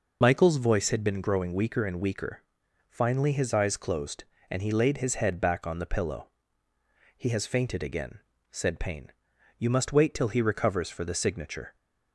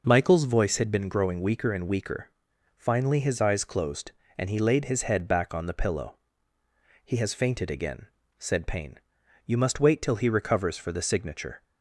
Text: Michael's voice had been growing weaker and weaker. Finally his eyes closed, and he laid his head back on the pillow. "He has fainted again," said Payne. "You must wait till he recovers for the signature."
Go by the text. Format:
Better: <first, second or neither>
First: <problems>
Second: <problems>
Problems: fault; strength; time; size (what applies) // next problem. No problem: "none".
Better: second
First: loses the start of "Michael's"; at 0.2 s; 40 ms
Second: none